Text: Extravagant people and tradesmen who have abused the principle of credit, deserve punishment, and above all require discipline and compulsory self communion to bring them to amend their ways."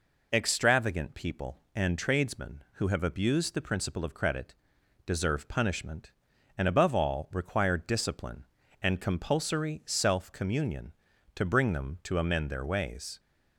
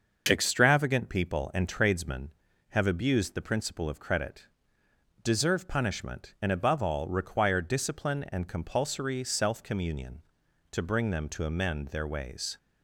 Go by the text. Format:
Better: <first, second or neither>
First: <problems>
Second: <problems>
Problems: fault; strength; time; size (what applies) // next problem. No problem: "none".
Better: first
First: none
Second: starts louder than the rest; until 1.2 s; 6 dB // skips "who"; at 2.5 s